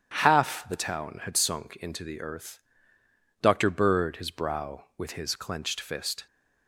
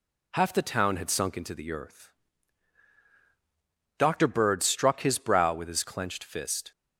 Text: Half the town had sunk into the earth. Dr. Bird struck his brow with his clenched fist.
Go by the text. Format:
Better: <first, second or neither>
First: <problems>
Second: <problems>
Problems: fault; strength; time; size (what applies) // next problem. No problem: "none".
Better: second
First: starts louder than the rest; strong; until 1.1 s; 9 dB // skips "struck"; at 4.1 s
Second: none